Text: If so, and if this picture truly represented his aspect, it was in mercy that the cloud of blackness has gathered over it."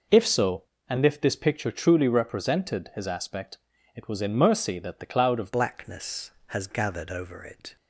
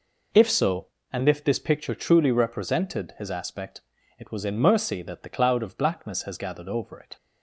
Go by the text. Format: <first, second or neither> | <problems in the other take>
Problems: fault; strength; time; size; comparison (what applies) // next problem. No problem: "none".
second | changes voice at "blackness"; from 5.5 s on; 2.2 s long